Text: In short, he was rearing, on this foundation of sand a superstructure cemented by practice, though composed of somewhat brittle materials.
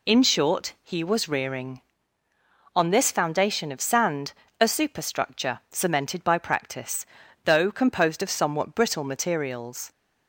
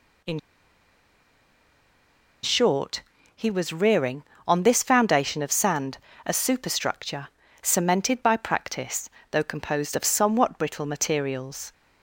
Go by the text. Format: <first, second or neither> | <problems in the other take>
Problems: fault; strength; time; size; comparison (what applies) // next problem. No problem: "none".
first | pauses between "In" and "short"; strong; at 0.3 s; 2.0 s long // pauses between "sand" and "a"; slight; at 5.9 s; 0.28 s long; slight in the first // pauses between "superstructure" and "cemented"; slight; at 7.2 s; 0.34 s long